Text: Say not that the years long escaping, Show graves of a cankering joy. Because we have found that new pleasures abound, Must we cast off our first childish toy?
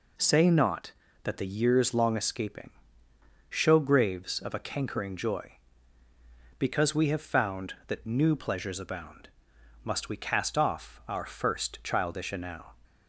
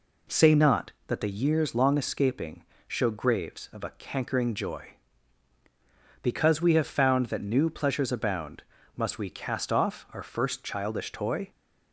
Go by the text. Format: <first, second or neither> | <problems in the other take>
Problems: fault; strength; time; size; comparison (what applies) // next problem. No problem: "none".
second | says "enow" for "toy"; at 12.3 s